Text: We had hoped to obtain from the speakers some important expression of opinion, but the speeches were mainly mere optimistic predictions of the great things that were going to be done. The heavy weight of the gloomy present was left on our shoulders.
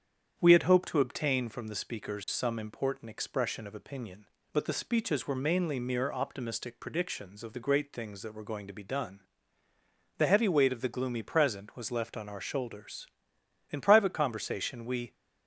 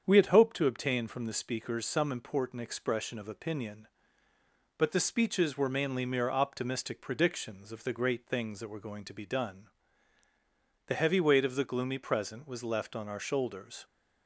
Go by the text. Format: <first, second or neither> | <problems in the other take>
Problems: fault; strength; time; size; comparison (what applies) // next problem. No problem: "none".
second | starts louder than the rest; strong; until 1.3 s; 8.5 dB; strong in the second // goes on to say "In private conversation we"; from 13.6 s on; 1.4 s long